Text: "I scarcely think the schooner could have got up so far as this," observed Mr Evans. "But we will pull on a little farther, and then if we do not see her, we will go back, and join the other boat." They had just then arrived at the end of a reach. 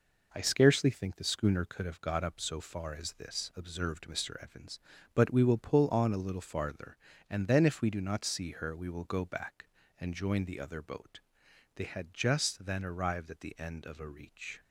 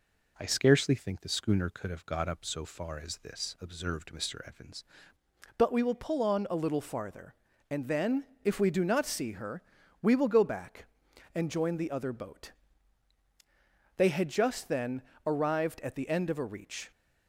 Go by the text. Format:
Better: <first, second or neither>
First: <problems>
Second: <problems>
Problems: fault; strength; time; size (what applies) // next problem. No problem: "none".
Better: first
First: none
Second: changes voice at "But"; from 5.5 s on; 11.4 s long // pauses between "then" and "if"; slight; at 8.2 s; 0.16 s long // pauses between "then" and "arrived"; slight; at 15.0 s; 0.22 s long